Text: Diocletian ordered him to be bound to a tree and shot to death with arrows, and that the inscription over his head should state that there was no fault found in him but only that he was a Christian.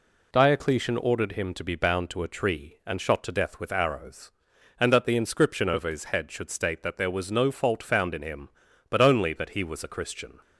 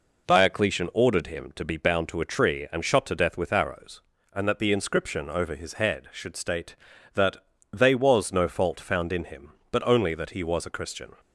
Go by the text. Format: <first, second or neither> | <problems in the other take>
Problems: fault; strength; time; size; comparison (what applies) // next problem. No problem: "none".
first | says "they" for "there"; at 7.7 s